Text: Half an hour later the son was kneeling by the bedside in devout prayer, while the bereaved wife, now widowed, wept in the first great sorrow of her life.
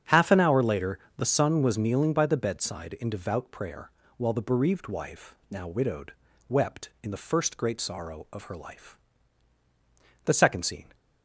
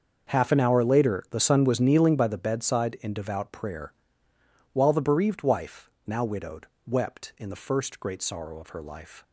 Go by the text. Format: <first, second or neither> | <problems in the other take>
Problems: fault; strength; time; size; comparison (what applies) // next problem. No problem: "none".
second | starts louder than the rest; strong; until 1.2 s; 8 dB; also in the second // pauses between "later" and "the"; slight; at 0.9 s; 0.18 s long // goes on to say "The second scene"; noticeable; from 10.2 s on; 0.68 s long